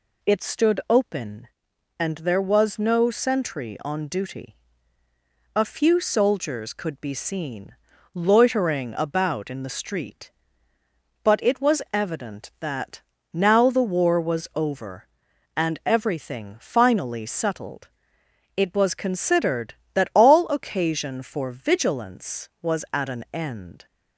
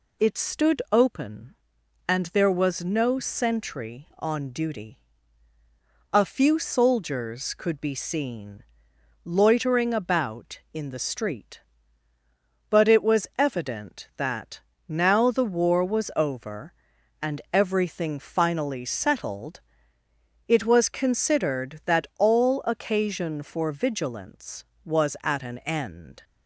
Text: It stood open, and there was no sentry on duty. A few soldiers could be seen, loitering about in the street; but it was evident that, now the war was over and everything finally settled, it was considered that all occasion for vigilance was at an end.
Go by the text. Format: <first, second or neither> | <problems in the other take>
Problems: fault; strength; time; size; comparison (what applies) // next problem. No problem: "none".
neither | none